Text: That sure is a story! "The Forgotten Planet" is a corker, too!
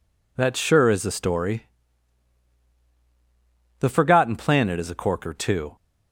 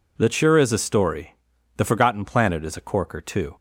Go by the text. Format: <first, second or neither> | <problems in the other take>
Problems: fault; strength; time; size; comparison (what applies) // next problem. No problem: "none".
neither | none